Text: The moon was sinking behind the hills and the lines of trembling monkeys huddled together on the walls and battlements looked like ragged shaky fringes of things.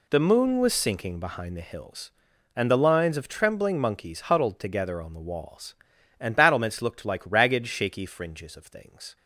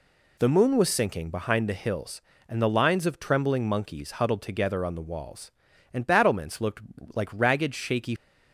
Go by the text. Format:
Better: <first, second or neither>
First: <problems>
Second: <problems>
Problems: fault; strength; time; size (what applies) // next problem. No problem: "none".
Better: first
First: none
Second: pauses between "looked" and "like"; slight; at 6.8 s; 0.34 s long // stops before "fringes of things"; at 8.1 s